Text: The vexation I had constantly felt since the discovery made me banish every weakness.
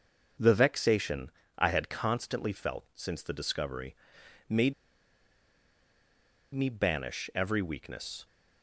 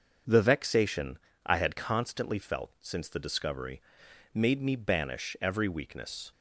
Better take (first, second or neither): second